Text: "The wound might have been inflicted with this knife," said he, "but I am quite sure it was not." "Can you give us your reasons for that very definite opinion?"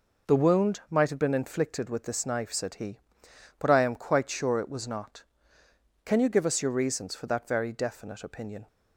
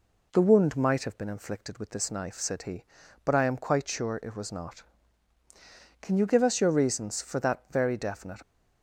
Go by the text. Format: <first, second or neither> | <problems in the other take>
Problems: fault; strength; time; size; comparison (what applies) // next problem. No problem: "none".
first | stops before "opinion"; at 8.4 s